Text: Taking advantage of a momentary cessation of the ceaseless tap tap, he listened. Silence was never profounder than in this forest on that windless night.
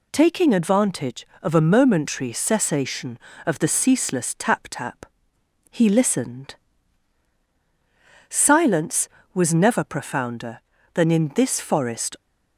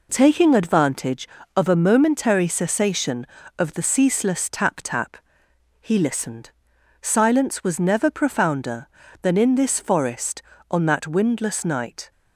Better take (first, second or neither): second